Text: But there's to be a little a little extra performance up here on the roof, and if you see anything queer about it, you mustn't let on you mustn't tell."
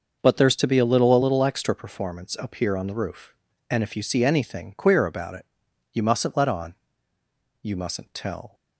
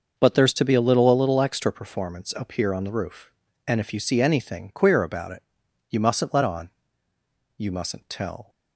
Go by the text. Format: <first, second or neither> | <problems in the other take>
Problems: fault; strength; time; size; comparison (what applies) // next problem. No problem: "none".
neither | starts louder than the rest; the same in both // pauses between "on" and "you"; noticeable; the same in both